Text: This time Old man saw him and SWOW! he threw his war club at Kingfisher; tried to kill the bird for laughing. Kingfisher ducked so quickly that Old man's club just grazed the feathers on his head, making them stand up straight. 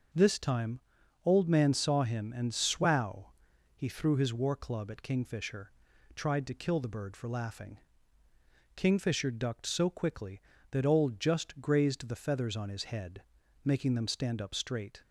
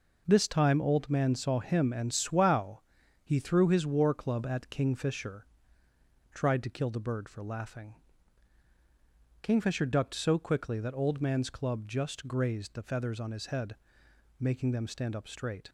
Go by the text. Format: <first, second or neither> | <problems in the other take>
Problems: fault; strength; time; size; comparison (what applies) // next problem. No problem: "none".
second | starts louder than the rest; noticeable; until 1.5 s; 6 dB // pauses between "time" and "Old"; at 0.7 s; 0.44 s long // skips "man's club"; at 11.1 s